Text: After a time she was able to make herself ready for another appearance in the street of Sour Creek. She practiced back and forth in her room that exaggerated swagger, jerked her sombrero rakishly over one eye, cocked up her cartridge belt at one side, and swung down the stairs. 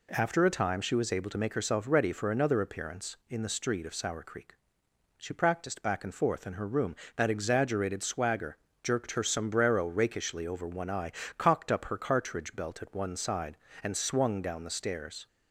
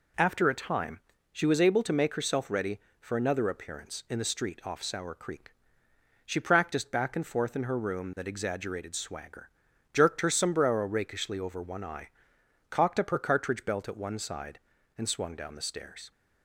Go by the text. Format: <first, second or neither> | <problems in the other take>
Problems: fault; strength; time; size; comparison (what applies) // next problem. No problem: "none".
first | pauses between "time" and "she"; slight; at 1.0 s; 0.32 s long // says "off" for "of"; at 4.6 s